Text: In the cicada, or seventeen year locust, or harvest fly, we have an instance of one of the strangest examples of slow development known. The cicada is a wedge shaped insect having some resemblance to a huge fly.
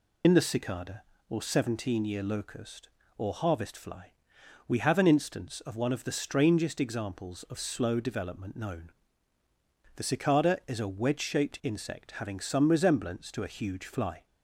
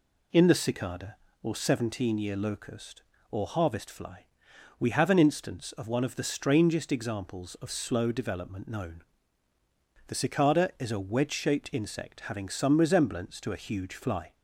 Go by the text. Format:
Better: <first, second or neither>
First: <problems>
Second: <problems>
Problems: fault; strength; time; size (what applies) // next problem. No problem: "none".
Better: second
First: loses the start of "In"; at 0.2 s; 70 ms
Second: none